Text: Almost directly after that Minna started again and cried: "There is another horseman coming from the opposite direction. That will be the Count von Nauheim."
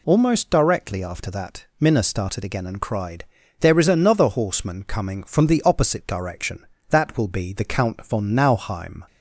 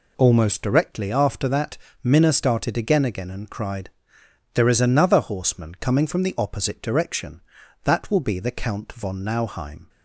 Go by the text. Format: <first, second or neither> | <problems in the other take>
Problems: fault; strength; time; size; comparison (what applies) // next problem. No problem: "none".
first | pauses between "that" and "Minna"; slight; at 1.7 s; 0.26 s long // says "again" twice; at 3.0 s